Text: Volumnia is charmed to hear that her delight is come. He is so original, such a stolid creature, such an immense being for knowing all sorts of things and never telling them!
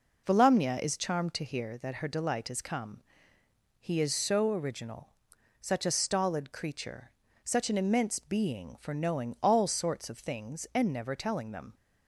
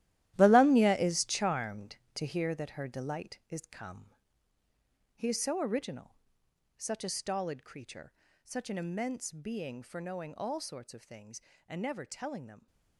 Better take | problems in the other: first | gets quieter; strong; throughout; 13.5 dB

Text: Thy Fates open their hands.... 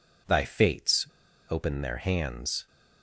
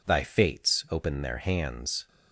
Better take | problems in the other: second | pauses between "Fates" and "open"; at 1.0 s; 0.42 s long

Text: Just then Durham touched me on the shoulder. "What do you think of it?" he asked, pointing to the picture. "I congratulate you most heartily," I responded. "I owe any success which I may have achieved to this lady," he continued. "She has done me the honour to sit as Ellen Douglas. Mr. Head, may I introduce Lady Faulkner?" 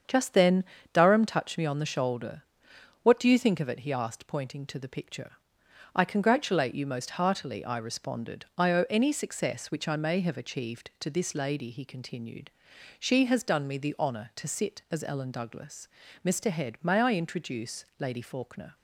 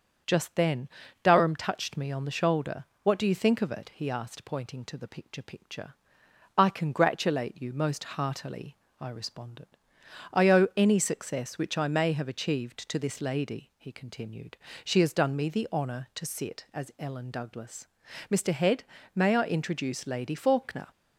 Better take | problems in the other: first | starts louder than the rest; until 1.6 s; 7 dB; strong in the first // pauses between "then" and "Durham"; slight; at 0.8 s; 0.34 s long; slight in the first // says "picture" twice; at 5.4 s

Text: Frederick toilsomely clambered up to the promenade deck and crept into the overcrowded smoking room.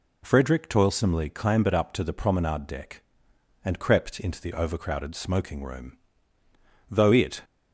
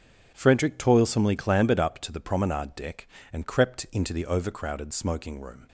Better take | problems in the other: second | goes on to say "Though it"; from 6.8 s on; 0.53 s long

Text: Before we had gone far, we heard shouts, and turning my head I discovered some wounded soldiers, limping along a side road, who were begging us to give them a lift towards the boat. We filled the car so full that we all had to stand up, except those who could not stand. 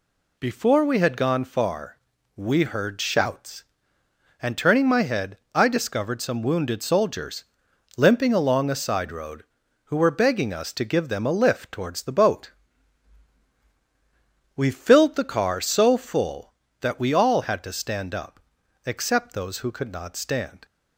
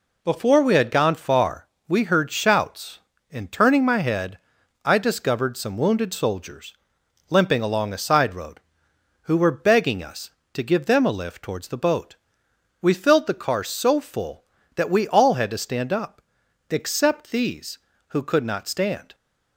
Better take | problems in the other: first | pauses between "head" and "I"; noticeable; at 4.3 s; 0.48 s long; slight in the first // says "these" for "those"; at 17.3 s

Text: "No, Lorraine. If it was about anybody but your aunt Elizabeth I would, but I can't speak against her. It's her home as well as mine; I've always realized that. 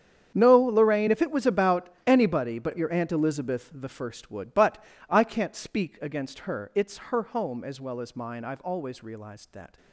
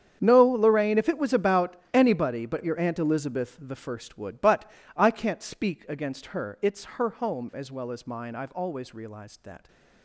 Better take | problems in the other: neither | starts louder than the rest; strong; the same in both // pauses between "about" and "anybody"; slight; the same in both // pauses between "but" and "I"; slight; the same in both

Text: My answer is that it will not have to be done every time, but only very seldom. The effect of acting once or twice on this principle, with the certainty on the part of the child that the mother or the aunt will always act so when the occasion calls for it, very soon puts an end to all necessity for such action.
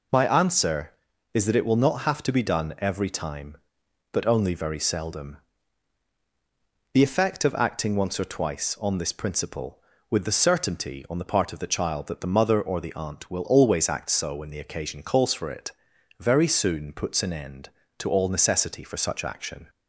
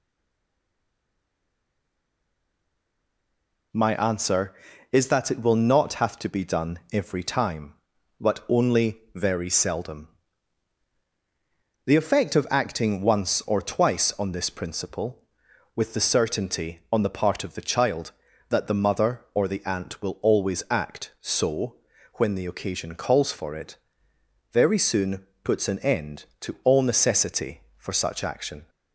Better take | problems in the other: first | stays silent before the first word; strong; until 3.7 s; 3.7 s long // pauses between "only" and "very"; slight; at 8.9 s; 0.16 s long // pauses between "so" and "when"; at 21.7 s; 0.40 s long // pauses between "soon" and "puts"; slight; at 25.2 s; 0.18 s long

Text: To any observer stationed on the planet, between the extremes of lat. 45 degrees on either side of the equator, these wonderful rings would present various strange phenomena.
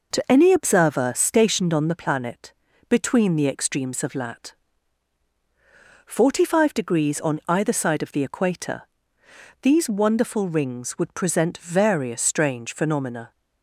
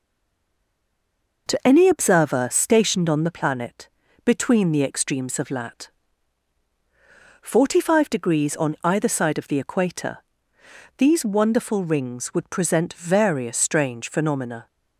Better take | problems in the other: first | stays silent before the first word; noticeable; until 1.4 s; 1.4 s long

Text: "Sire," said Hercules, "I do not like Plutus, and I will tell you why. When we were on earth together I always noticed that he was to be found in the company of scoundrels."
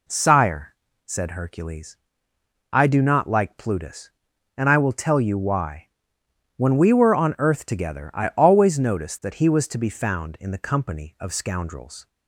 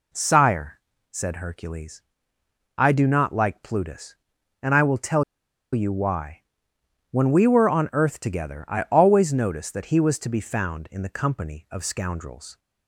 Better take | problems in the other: first | pauses between "tell" and "you"; noticeable; at 5.2 s; 0.49 s long

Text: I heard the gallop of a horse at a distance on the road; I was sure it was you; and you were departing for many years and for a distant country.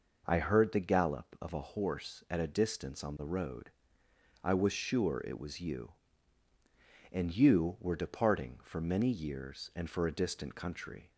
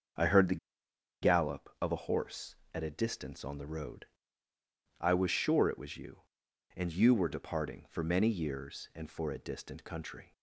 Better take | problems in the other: first | starts louder than the rest; until 1.9 s; 6.5 dB // pauses between "the" and "gallop"; noticeable; at 0.5 s; 0.65 s long

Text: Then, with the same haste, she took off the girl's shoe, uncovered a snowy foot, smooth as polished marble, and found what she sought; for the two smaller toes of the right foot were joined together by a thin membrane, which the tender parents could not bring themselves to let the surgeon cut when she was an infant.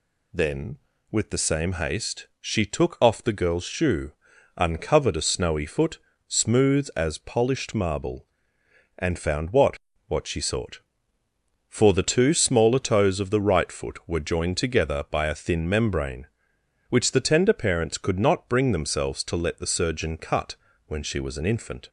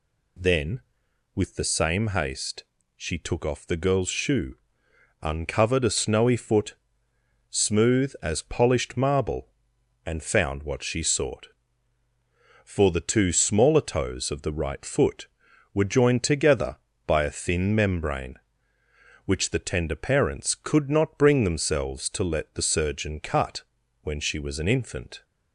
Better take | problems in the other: second | says "what" twice; at 10.0 s // pauses between "cut" and "when"; slight; at 20.5 s; 0.30 s long; also in the second

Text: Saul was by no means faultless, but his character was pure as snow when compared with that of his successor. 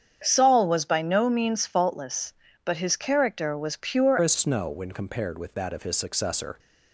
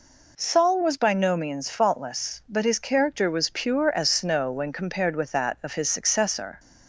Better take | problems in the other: second | starts louder than the rest; strong; until 1.2 s; 8 dB // changes voice at "as"; from 4.2 s on; 2.3 s long

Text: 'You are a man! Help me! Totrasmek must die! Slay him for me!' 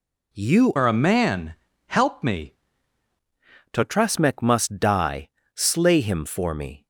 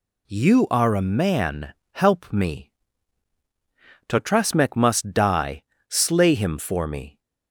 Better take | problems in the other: second | changes voice from "are" to "me"; from 0.7 to 2.5 s; 1.8 s long

